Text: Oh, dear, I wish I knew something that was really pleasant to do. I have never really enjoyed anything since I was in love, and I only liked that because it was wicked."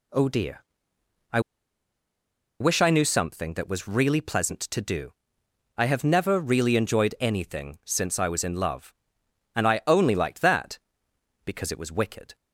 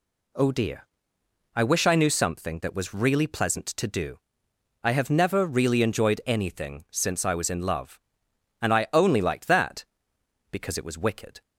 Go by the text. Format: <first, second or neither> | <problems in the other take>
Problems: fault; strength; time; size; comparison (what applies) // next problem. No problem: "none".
second | pauses between "I" and "wish"; at 1.3 s; 1.2 s long